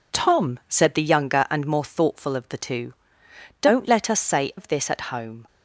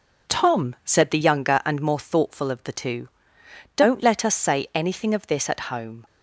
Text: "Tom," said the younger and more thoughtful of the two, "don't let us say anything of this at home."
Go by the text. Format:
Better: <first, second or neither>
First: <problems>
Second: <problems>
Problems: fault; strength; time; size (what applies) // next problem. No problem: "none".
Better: second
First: skips "anything"; at 4.5 s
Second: none